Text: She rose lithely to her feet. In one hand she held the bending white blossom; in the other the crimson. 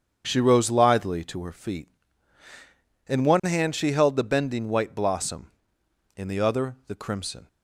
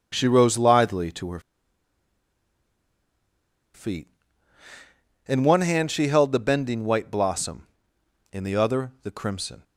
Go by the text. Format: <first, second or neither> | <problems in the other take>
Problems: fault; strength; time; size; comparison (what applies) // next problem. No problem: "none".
first | starts louder than the rest; strong; until 1.1 s; 7.5 dB; strong in the first // pauses between "her" and "feet"; strong; at 1.3 s; 2.3 s long